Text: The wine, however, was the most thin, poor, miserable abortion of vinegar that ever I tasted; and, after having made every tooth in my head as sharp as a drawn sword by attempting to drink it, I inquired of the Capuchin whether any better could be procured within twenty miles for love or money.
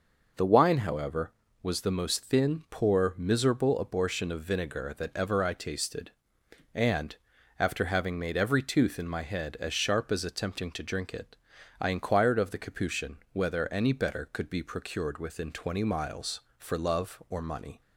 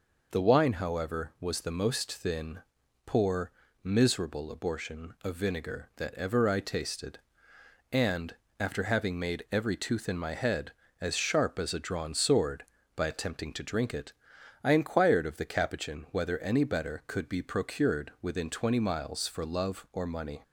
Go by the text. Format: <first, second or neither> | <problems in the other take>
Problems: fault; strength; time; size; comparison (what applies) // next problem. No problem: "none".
second | skips "a drawn sword by"; at 10.2 s